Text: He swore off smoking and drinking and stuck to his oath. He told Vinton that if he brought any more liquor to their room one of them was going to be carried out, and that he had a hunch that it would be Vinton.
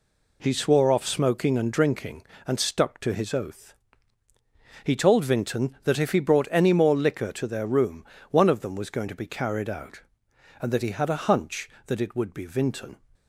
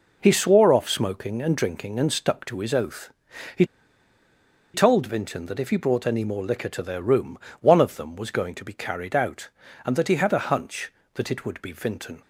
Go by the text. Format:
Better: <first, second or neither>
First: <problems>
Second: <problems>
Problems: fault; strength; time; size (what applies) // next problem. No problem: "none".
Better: first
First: pauses between "room" and "one"; slight; at 8.0 s; 0.28 s long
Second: pauses between "He" and "told"; at 3.6 s; 1.1 s long // pauses between "room" and "one"; slight; at 7.3 s; 0.20 s long